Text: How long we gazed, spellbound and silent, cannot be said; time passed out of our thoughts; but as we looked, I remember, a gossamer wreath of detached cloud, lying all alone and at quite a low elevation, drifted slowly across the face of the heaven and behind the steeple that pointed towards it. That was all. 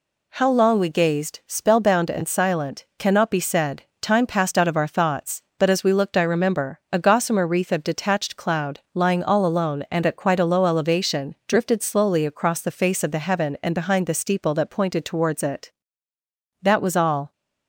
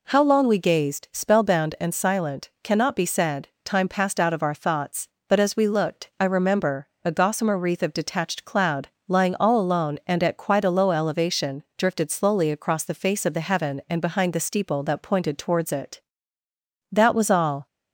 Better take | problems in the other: neither | none

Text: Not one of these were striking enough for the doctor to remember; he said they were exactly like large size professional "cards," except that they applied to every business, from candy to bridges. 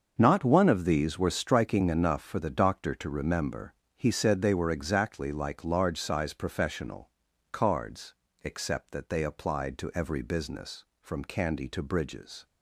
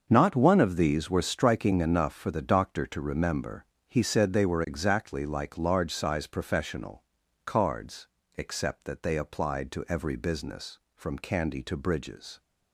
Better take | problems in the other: neither | starts louder than the rest; the same in both // pauses between "professional" and "cards"; the same in both

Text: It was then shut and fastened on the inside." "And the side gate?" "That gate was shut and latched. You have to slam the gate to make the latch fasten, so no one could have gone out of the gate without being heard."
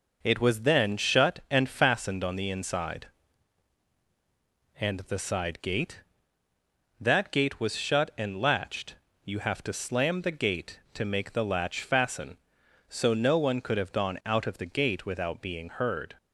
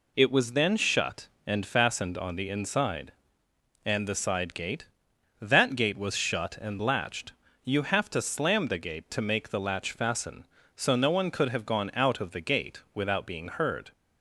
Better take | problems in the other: neither | none

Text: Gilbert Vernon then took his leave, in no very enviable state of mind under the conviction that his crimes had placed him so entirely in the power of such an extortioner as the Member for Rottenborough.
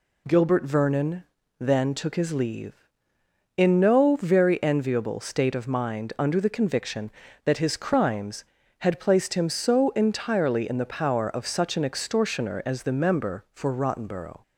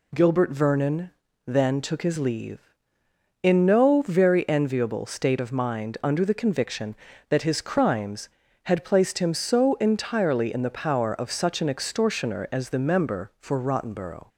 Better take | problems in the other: neither | pauses between "Vernon" and "then"; slight; the same in both

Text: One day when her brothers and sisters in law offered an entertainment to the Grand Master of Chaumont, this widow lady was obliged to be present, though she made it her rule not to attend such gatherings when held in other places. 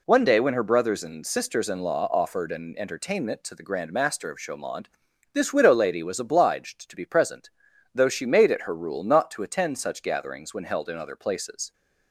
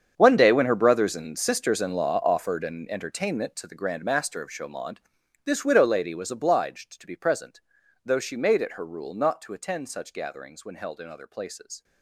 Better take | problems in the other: first | gets quieter; strong; throughout; 16 dB

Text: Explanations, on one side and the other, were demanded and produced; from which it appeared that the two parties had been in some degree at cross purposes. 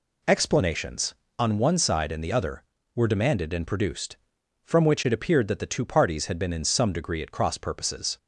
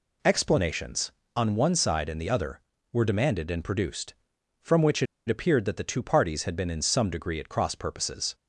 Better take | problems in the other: first | pauses between "it" and "appeared"; slight; at 5.0 s; 0.22 s long

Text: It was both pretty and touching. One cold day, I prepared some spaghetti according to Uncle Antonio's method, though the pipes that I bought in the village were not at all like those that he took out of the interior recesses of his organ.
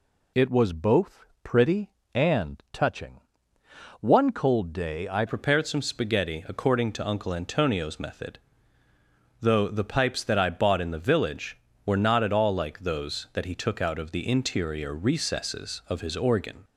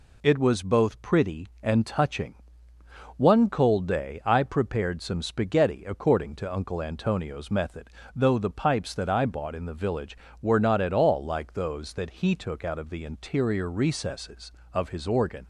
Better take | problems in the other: second | pauses between "both" and "pretty"; slight; at 1.2 s; 0.18 s long // changes voice at "prepared"; from 5.2 s on; 11.4 s long

